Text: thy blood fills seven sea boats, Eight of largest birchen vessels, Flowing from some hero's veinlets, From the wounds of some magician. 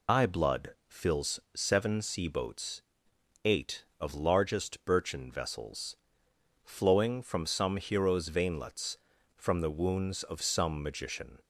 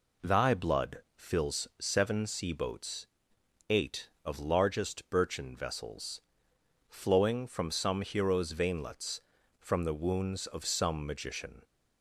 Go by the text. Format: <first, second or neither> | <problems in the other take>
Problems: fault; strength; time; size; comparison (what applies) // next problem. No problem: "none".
second | loses the start of "thy"; at 0.0 s; 150 ms // pauses between "fills" and "seven"; slight; at 1.3 s; 0.15 s long